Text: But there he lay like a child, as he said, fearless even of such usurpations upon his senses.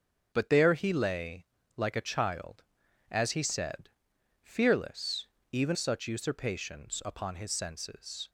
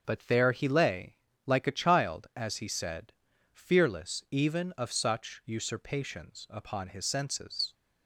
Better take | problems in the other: second | starts louder than the rest; noticeable; until 1.3 s; 6 dB; also in the second // pauses between "lay" and "like"; slight; at 1.4 s; 0.30 s long; slight in the second // pauses between "fearless" and "even"; slight; at 5.2 s; 0.24 s long // skips "of"; at 5.7 s

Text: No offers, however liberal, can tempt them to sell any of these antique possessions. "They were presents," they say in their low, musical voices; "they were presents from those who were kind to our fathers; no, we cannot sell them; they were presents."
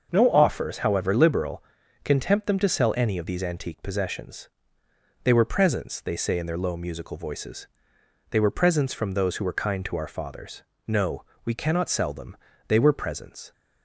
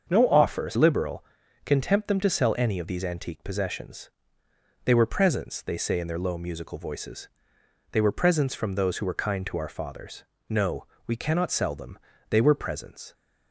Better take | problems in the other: first | starts louder than the rest; until 1.1 s; 6.5 dB; also in the first // skips "however"; at 0.7 s

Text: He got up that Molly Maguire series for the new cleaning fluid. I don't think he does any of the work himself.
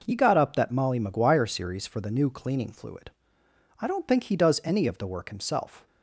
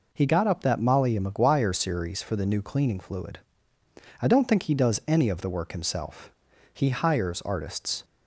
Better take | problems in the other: first | goes on to say "He hires artists"; noticeable; from 6.7 s on; 1.3 s long

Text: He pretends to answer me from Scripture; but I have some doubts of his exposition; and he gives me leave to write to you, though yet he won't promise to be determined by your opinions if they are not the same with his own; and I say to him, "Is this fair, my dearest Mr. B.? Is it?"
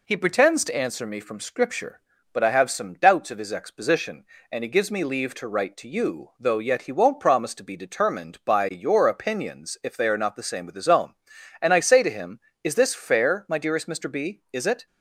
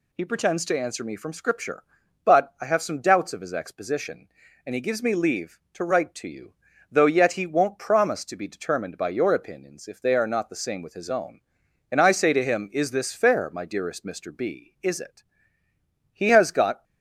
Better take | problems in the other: first | goes on to say "He has got"; noticeable; from 16.1 s on; 0.72 s long

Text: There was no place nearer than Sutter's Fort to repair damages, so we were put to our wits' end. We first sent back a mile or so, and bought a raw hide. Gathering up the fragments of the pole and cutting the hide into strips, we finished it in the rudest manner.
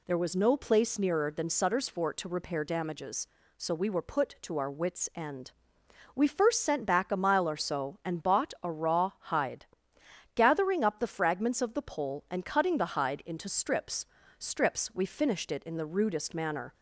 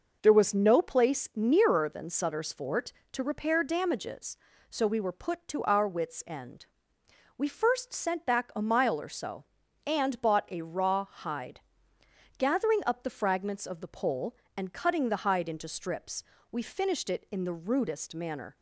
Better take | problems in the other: second | says "strips" twice; at 14.3 s

